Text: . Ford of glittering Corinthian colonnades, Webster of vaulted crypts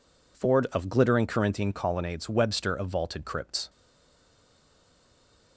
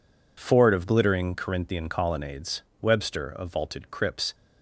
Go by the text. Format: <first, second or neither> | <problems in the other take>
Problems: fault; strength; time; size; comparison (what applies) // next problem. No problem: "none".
second | stays silent after the last word; noticeable; from 3.6 s on; 1.9 s long